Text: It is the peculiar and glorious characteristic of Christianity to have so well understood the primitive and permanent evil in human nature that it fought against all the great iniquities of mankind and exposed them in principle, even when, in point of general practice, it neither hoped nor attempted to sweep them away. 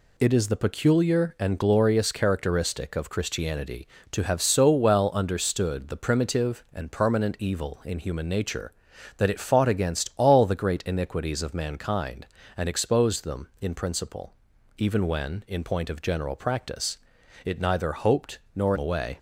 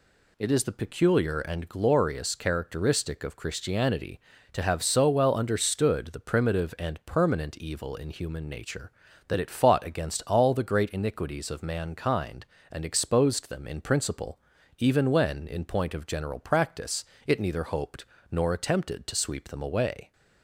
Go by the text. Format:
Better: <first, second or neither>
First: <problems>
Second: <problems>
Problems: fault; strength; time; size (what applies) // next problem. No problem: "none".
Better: second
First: pauses between "hoped" and "nor"; slight; at 18.3 s; 0.16 s long // skips "attempted to sweep them"; at 18.7 s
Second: pauses between "hoped" and "nor"; slight; at 18.0 s; 0.24 s long